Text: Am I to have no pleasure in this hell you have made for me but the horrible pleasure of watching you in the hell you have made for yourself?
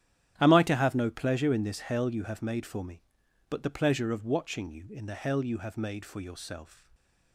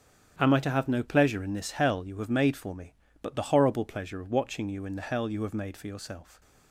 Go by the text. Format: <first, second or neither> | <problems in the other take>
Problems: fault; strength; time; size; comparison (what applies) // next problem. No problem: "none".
second | starts louder than the rest; strong; until 1.3 s; 10.5 dB; strong in the second // skips "horrible"; at 3.6 s